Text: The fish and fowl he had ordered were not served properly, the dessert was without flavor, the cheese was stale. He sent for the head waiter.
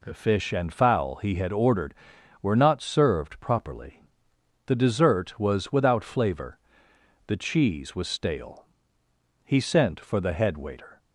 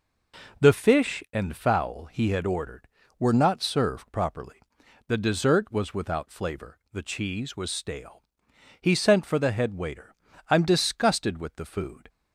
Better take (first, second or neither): first